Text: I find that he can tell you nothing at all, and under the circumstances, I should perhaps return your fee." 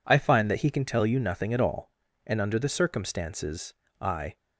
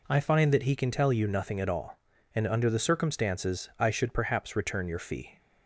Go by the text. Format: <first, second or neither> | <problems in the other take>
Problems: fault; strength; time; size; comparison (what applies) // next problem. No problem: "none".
second | stops before "should perhaps return your fee"; at 4.3 s